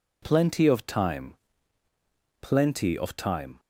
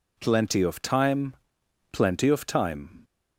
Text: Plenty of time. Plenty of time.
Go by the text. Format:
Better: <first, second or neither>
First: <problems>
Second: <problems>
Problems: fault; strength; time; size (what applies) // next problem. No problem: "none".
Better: neither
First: none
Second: none